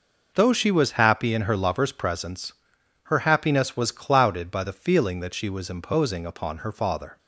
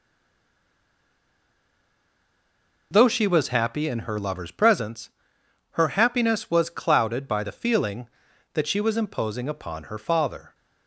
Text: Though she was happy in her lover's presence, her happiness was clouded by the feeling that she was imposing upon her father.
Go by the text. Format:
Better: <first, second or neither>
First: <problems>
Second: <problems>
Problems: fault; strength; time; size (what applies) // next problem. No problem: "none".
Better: first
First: none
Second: stays silent before the first word; strong; until 2.9 s; 2.9 s long